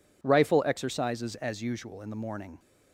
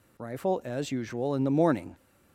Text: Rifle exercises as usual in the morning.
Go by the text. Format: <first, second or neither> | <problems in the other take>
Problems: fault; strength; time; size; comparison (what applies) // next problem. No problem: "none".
first | skips "exercises"; at 0.6 s